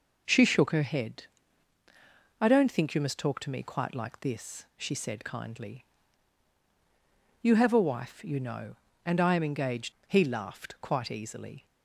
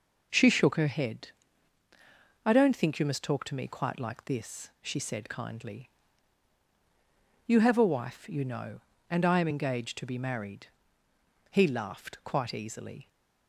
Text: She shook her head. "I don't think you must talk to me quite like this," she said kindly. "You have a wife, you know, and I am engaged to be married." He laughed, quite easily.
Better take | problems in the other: second | skips "to be married"; at 9.9 s

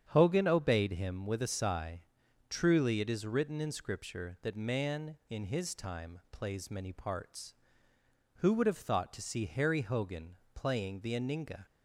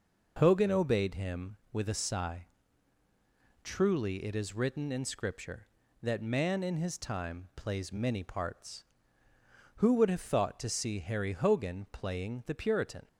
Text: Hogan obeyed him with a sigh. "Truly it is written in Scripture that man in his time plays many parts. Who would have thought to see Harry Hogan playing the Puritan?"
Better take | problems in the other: second | starts louder than the rest; strong; until 1.1 s; 8.5 dB // pauses between "Hogan" and "playing"; slight; at 10.3 s; 0.16 s long // says "Aninga" for "Puritan"; at 11.1 s

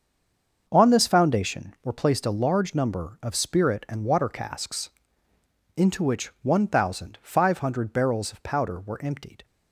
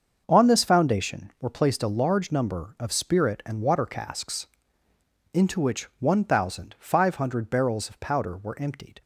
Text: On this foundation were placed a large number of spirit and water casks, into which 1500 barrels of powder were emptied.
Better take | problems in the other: second | stays silent before the first word; slight; until 0.6 s; 0.6 s long // starts louder than the rest; until 1.6 s; 6.5 dB; also in the second

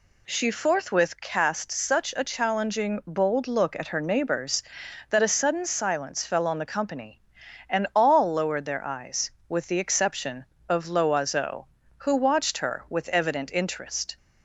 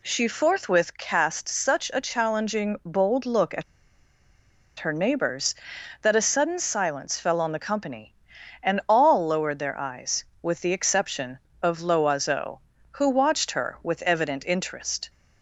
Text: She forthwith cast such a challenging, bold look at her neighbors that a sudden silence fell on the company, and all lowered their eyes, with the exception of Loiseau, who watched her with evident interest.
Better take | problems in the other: first | pauses between "at" and "her"; at 3.6 s; 1.1 s long

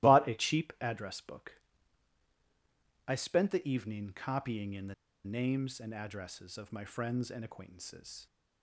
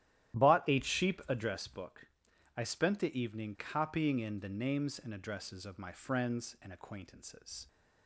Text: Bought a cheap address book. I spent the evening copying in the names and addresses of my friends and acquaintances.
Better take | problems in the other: second | starts louder than the rest; strong; until 1.1 s; 16 dB; strong in the second // pauses between "the" and "names"; slight; at 4.9 s; 0.30 s long

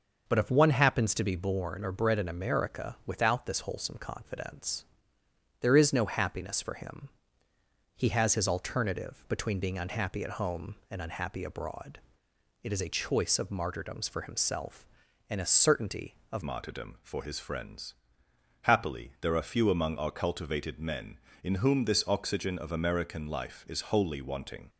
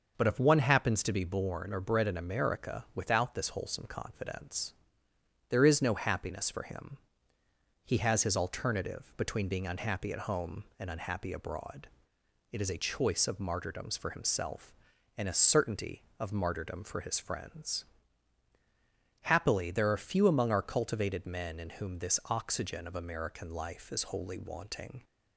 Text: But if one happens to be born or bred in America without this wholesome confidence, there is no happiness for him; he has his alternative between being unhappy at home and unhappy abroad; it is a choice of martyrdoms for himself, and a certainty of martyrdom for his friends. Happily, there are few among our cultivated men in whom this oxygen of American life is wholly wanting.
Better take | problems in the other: second | starts louder than the rest; until 1.2 s; 6 dB; also in the second // changes voice at "martyrdom"; from 16.4 s on; 8.2 s long

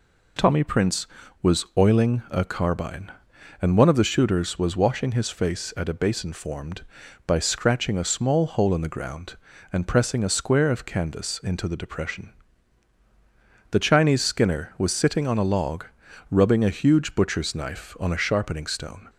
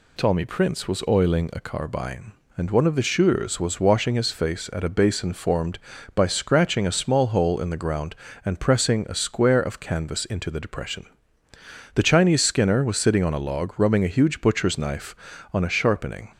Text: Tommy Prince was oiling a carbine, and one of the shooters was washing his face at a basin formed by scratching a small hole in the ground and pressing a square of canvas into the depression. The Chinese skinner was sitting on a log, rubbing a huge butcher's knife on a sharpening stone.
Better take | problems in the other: first | stops before "stone"; at 16.3 s

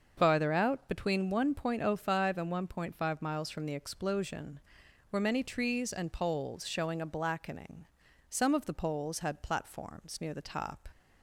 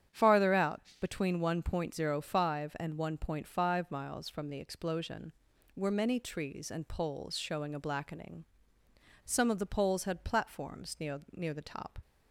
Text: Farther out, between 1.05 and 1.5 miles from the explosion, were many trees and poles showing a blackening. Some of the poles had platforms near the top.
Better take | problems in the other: first | starts louder than the rest; strong; until 1.3 s; 9 dB; also in the first // says "near" twice; at 11.3 s

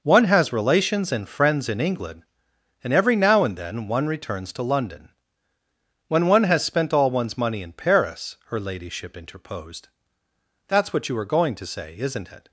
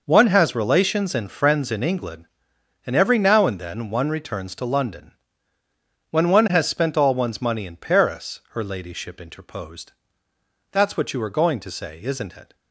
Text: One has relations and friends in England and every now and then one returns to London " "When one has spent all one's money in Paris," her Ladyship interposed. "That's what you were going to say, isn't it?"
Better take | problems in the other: neither | none

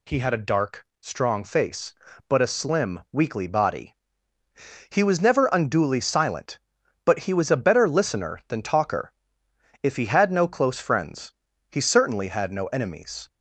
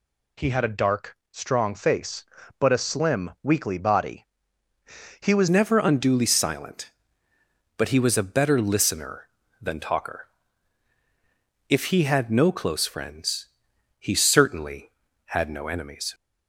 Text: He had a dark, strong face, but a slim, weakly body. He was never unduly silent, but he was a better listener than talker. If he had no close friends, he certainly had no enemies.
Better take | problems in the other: first | changes voice at "never"; from 5.4 s on; 10.7 s long

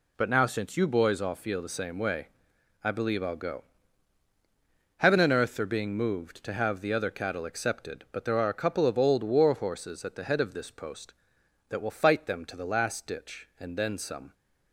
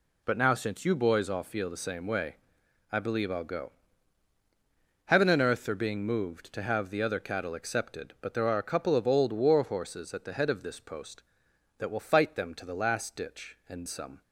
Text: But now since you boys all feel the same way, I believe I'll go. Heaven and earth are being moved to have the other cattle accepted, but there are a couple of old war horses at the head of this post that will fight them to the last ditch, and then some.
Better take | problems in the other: first | skips "then"; at 13.8 s

